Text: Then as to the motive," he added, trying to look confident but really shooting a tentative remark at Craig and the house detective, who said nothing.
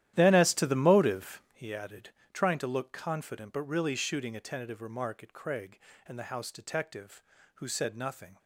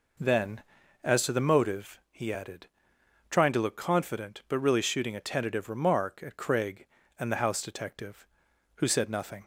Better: second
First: starts louder than the rest; strong; until 1.6 s; 12.5 dB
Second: none

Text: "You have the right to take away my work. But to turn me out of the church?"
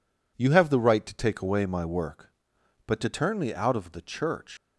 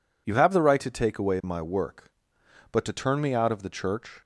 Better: second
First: leaves "church" unfinished; at 4.5 s; 95 ms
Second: none

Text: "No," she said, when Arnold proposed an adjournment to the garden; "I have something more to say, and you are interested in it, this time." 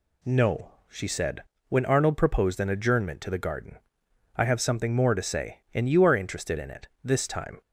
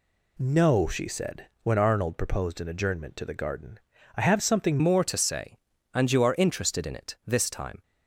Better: first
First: none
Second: changes voice at "more"; from 4.8 s on; 3.0 s long

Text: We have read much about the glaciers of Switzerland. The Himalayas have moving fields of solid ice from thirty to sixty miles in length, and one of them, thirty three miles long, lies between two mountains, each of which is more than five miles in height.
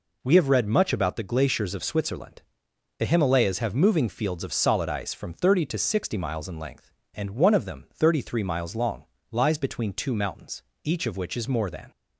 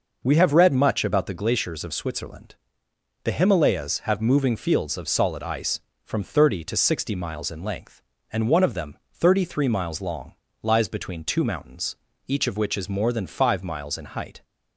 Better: second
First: stops before "five miles in height"; at 11.9 s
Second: none

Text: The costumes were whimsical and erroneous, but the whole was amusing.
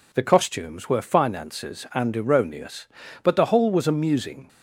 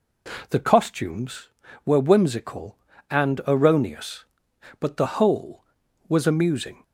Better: second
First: says "finances" for "whimsical"; at 1.0 s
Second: none

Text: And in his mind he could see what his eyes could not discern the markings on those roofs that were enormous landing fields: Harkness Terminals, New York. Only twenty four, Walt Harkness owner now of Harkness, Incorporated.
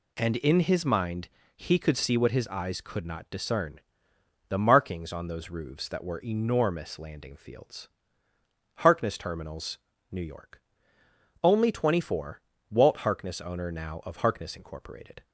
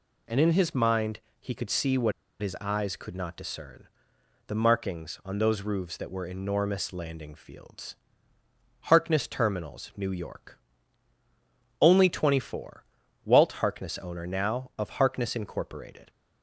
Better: first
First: pauses between "mind" and "he"; slight; at 1.2 s; 0.28 s long // pauses between "discern" and "the"; noticeable; at 3.7 s; 0.70 s long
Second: pauses between "mind" and "he"; slight; at 1.2 s; 0.20 s long // pauses between "what" and "his"; slight; at 2.1 s; 0.29 s long // pauses between "discern" and "the"; noticeable; at 3.8 s; 0.64 s long

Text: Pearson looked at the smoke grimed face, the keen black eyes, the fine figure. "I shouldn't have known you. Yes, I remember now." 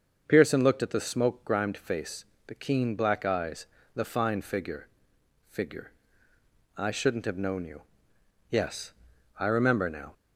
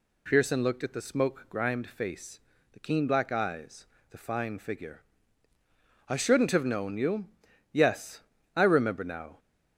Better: second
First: starts louder than the rest; until 1.2 s; 6.5 dB // says "figure" twice; at 5.5 s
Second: none

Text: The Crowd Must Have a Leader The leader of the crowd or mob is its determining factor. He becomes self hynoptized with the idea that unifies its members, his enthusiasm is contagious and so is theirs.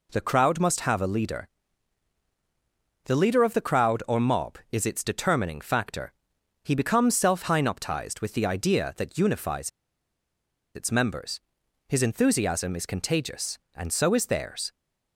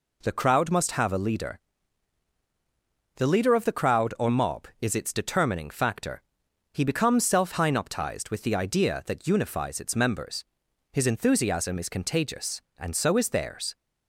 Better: second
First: pauses between "Leader" and "The"; strong; at 1.4 s; 1.5 s long // pauses between "unifies" and "its"; at 9.6 s; 1.0 s long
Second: pauses between "Leader" and "The"; strong; at 1.5 s; 1.5 s long

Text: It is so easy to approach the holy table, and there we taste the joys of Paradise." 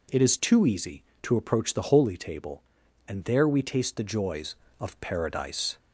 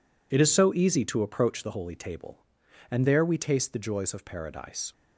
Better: second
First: says "too" for "so"; at 0.4 s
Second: none

